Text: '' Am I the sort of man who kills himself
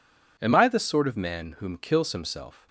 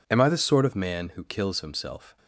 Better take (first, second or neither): second